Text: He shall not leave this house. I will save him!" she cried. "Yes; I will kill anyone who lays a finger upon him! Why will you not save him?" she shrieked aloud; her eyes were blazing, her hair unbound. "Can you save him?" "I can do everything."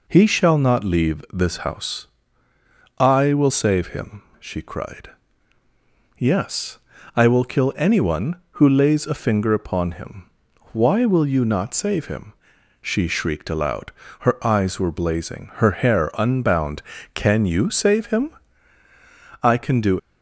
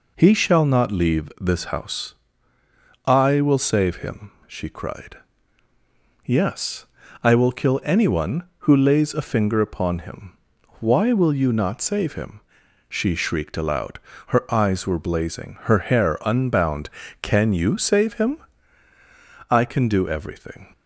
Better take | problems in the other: second | stops before "everything"; at 19.9 s

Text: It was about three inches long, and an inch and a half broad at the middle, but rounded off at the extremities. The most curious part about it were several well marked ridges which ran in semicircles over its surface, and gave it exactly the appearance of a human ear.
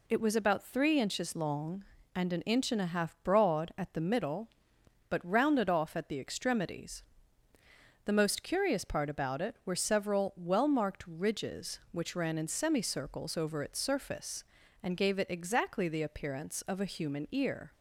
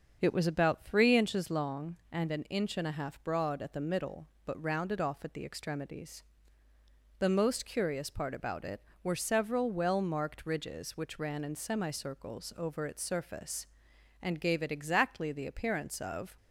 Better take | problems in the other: first | starts louder than the rest; until 1.2 s; 6.5 dB // stops before "a human ear"; at 16.3 s

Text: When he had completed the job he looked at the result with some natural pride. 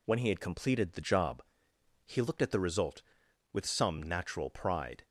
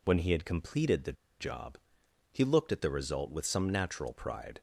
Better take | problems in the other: first | pauses between "the" and "job"; slight; at 1.1 s; 0.27 s long // pauses between "job" and "he"; noticeable; at 1.7 s; 0.56 s long; noticeable in the first

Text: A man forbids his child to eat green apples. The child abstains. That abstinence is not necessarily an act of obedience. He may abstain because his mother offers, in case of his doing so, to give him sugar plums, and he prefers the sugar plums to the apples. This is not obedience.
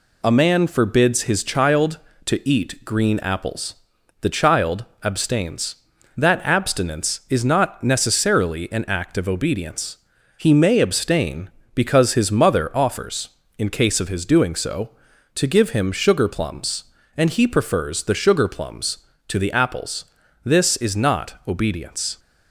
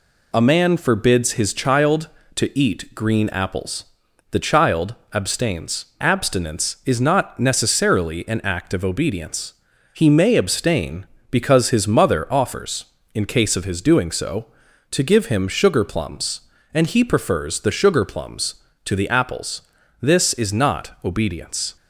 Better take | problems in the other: first | pauses between "child" and "abstains"; slight; at 4.9 s; 0.18 s long; slight in the first // skips "That"; at 5.9 s

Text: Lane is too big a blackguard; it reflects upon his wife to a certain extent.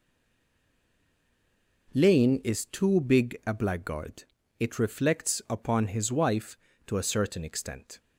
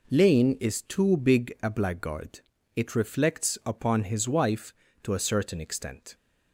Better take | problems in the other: second | stays silent before the first word; noticeable; until 1.8 s; 1.8 s long

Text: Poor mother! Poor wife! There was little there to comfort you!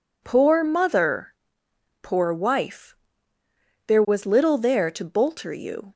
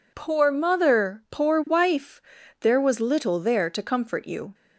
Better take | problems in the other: second | says "bolter" for "comfort"; at 5.0 s

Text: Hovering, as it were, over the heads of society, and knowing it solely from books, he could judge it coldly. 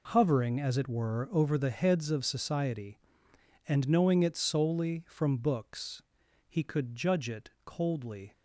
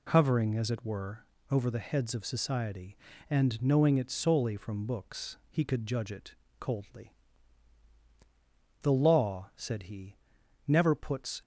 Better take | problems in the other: first | pauses between "it" and "coldly"; slight; at 6.3 s; 0.26 s long // goes on to say "The law said he never puts"; strong; from 8.8 s on; 2.5 s long

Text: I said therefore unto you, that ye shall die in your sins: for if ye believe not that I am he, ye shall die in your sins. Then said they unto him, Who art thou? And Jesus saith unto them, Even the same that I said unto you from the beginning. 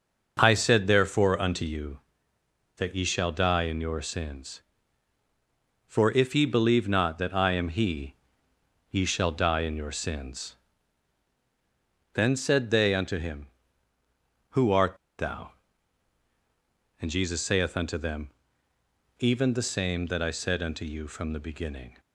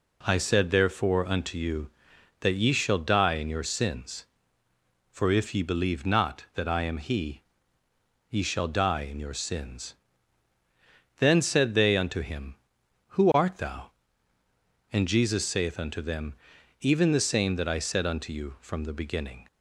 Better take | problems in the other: second | starts louder than the rest; noticeable; until 1.4 s; 6 dB // pauses between "art" and "thou"; slight; at 14.9 s; 0.22 s long

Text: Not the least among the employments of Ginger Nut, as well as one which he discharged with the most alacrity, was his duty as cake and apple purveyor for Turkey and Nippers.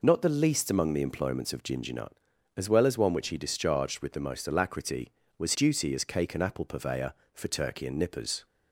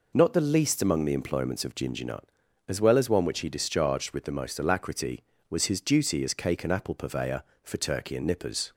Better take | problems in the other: second | skips "his"; at 5.5 s

